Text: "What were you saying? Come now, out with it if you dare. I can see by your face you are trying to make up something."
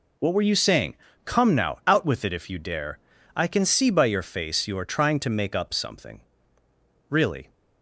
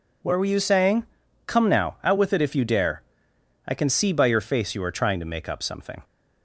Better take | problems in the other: second | goes on to say "Really"; slight; from 7.1 s on; 0.40 s long

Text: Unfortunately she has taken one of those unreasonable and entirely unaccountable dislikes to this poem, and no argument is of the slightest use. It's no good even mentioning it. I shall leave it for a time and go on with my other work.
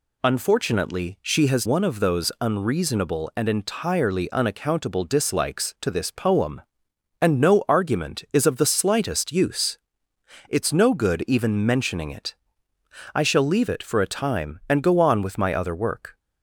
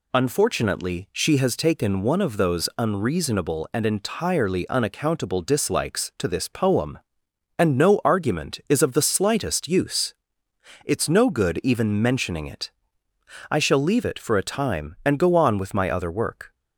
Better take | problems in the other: second | skips "taken"; at 1.6 s

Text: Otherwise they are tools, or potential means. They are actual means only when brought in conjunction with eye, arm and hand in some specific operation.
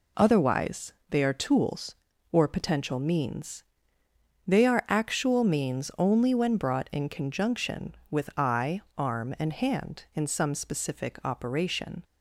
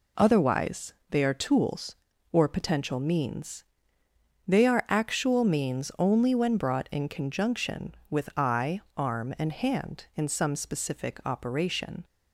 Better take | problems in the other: neither | pauses between "Otherwise" and "they"; slight; the same in both

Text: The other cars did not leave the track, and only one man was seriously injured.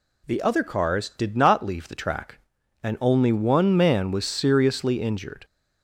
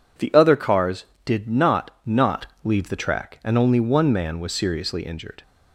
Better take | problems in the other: first | says "not" twice; at 2.0 s

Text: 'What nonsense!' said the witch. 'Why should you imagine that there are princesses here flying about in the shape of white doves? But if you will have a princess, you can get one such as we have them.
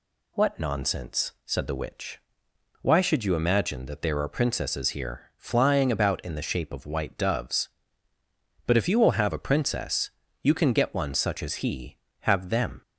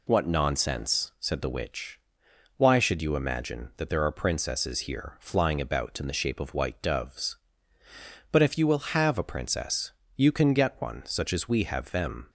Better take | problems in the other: second | says "he" for "we"; at 11.5 s

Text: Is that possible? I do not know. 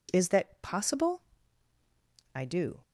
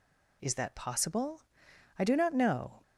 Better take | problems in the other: second | stops before "not know"; at 2.8 s

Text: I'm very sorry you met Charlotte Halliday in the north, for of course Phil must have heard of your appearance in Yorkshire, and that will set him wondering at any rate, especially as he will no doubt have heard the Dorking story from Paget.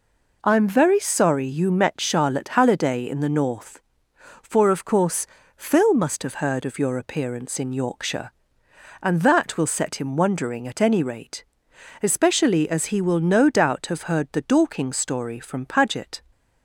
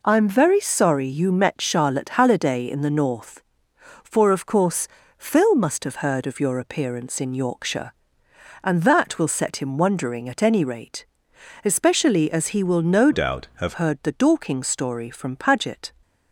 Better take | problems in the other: first | pauses between "course" and "Phil"; slight; at 4.8 s; 0.32 s long; slight in the first // changes voice from "doubt" to "have"; from 13.1 to 13.7 s; 0.6 s long

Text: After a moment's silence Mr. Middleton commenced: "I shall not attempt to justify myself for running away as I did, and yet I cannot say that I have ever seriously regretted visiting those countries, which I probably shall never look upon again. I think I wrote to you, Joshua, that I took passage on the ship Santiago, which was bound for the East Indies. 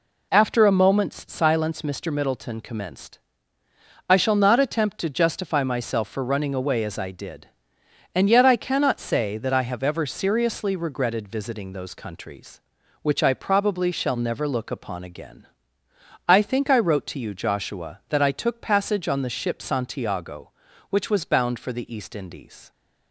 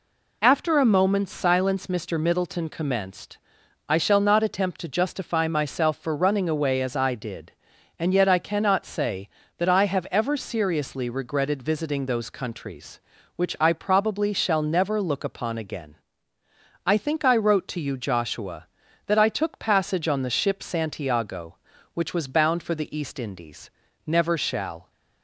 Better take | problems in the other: first | goes on to say "Never shall"; noticeable; from 24.0 s on; 0.84 s long

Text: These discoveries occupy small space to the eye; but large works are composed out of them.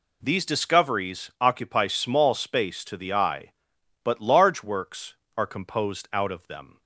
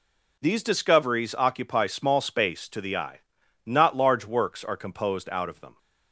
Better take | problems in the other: first | says "not" for "but"; at 3.6 s

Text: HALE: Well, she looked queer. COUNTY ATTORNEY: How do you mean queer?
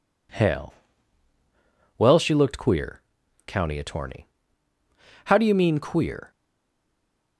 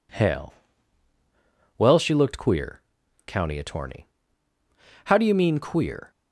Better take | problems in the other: second | stays silent after the last word; from 6.3 s on; 1.0 s long

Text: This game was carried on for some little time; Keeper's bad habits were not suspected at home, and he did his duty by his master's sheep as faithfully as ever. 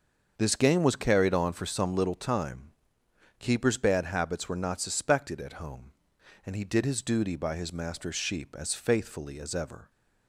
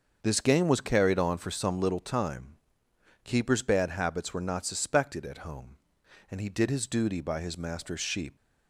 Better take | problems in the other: first | starts louder than the rest; until 1.2 s; 6.5 dB; also in the first // stops before "as faithfully as ever"; at 8.3 s

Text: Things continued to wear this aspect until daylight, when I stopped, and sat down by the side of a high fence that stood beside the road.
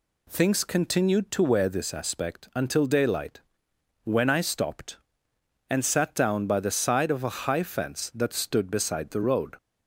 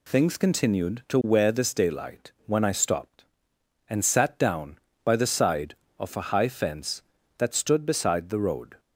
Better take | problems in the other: first | skips "aspect until"; at 1.7 s

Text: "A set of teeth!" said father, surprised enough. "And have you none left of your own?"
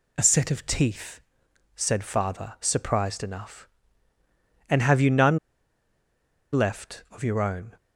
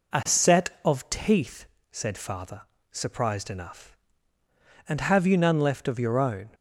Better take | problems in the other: second | pauses between "none" and "left"; at 5.3 s; 1.1 s long

